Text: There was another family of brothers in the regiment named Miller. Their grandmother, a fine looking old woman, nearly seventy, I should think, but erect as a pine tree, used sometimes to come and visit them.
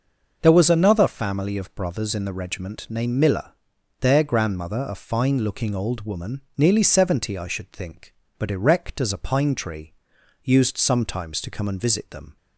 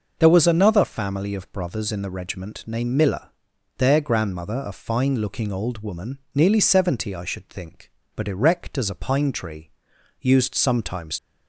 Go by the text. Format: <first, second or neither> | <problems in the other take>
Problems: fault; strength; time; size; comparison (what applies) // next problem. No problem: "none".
first | stops before "to come and visit them"; at 11.1 s